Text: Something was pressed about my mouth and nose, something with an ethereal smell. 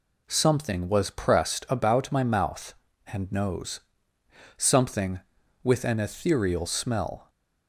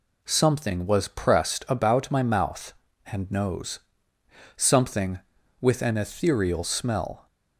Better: neither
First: none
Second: none

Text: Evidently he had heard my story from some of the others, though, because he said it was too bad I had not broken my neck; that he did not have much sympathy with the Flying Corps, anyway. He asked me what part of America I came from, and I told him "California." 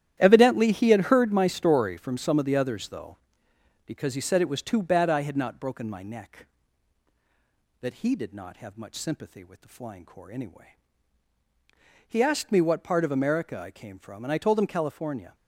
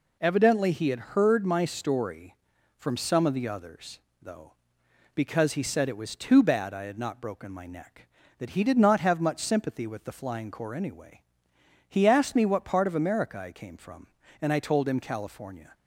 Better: second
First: gets quieter; strong; throughout; 11.5 dB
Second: none

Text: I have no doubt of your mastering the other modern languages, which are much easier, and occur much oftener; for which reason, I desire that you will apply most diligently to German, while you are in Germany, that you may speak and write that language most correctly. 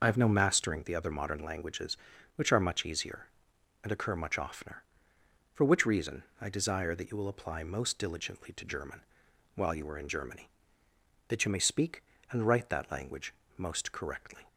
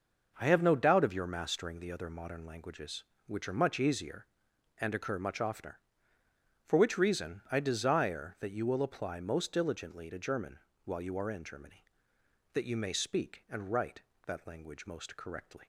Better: second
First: skips "doubt of your"; at 0.2 s // pauses between "language" and "most"; slight; at 13.3 s; 0.24 s long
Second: none

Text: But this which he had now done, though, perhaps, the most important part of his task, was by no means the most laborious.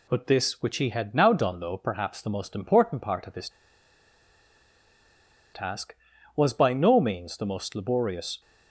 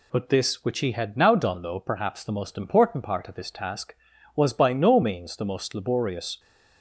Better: second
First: pauses between "his" and "task"; strong; at 3.4 s; 2.0 s long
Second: none

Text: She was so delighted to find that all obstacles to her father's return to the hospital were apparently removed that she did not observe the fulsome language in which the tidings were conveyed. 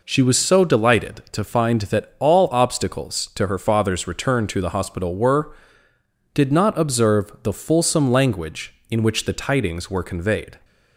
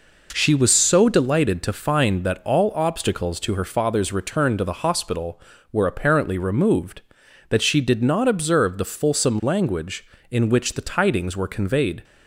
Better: second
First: skips "apparently removed that she"; at 5.9 s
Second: none

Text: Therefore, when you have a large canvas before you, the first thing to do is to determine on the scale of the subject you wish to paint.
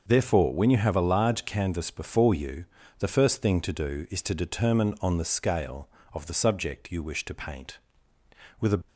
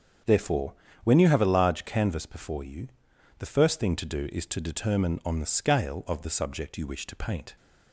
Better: second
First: starts louder than the rest; noticeable; until 1.0 s; 6 dB // goes on to say "With a"; slight; from 8.6 s on; 0.26 s long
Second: starts louder than the rest; strong; until 1.5 s; 7.5 dB

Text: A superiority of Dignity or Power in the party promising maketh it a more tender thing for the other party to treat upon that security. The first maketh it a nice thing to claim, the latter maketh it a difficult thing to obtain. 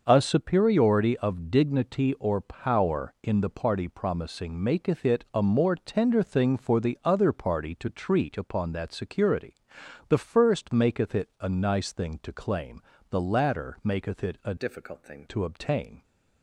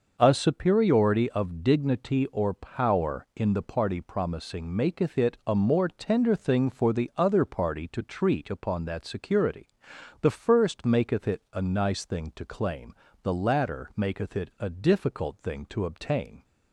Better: second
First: starts louder than the rest; noticeable; until 1.0 s; 6 dB // changes voice from "difficult" to "thing"; from 14.5 to 15.2 s; 0.7 s long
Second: starts louder than the rest; noticeable; until 1.2 s; 6 dB

